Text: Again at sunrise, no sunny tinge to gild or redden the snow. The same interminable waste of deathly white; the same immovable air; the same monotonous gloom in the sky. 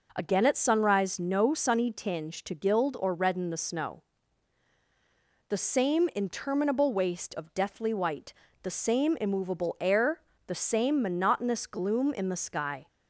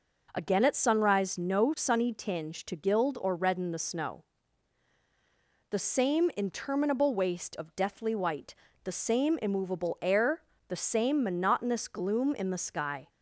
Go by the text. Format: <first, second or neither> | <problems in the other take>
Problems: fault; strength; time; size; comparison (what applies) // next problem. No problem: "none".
neither | none